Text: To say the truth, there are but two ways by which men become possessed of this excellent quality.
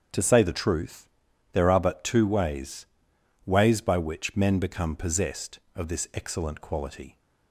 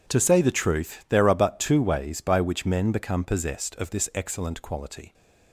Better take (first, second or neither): second